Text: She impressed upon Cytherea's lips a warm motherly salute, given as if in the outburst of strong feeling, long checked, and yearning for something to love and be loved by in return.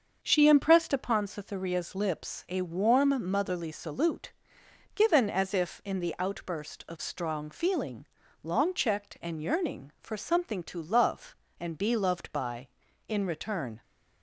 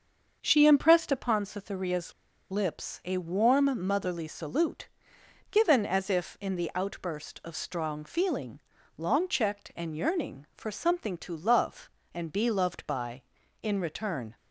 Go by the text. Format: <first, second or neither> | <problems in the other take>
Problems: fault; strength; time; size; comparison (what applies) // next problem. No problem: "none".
first | starts louder than the rest; until 1.4 s; 6.5 dB; also in the first // pauses between "Cytherea's" and "lips"; at 2.1 s; 0.39 s long